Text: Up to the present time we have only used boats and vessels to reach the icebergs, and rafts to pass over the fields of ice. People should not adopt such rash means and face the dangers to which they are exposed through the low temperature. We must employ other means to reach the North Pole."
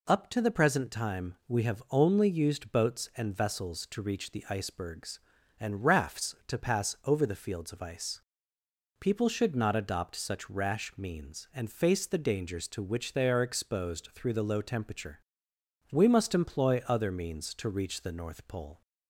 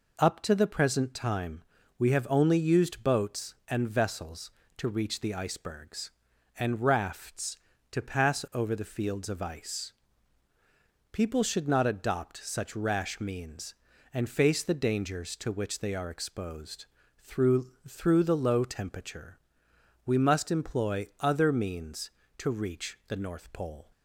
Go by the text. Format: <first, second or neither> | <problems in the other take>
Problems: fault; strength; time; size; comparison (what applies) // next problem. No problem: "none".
first | pauses between "time" and "we"; slight; at 1.6 s; 0.36 s long // pauses between "exposed" and "through"; slight; at 16.8 s; 0.34 s long // says "through" twice; at 17.8 s